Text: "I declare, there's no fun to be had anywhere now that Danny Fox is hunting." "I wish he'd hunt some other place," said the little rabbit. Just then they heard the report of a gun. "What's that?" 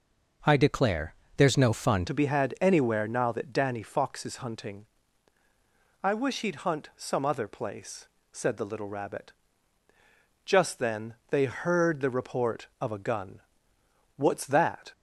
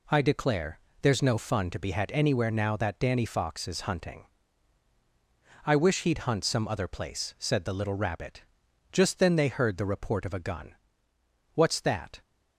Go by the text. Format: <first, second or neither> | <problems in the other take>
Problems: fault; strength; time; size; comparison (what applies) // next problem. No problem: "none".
second | changes voice at "to"; from 2.0 s on; 12.9 s long // pauses between "then" and "they"; slight; at 11.1 s; 0.16 s long